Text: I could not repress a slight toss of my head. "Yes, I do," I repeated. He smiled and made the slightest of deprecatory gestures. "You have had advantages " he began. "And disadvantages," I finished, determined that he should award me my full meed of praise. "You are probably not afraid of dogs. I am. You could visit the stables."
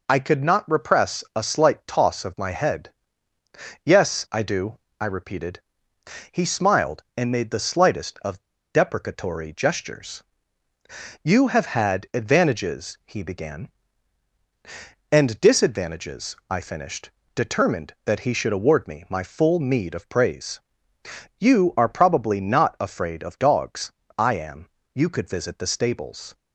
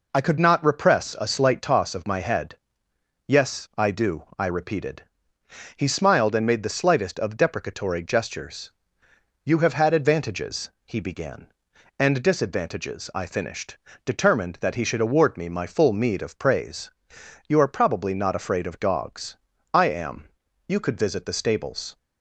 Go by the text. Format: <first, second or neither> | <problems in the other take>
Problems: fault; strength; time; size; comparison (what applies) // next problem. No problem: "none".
second | pauses between "of" and "deprecatory"; slight; at 8.4 s; 0.29 s long